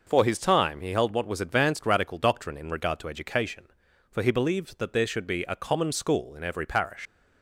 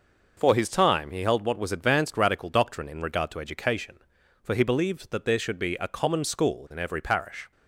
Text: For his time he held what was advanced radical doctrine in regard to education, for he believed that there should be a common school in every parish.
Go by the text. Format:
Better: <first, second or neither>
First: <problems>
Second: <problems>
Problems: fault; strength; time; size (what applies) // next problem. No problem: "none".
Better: second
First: leaves "parish" unfinished; at 7.0 s; 105 ms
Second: none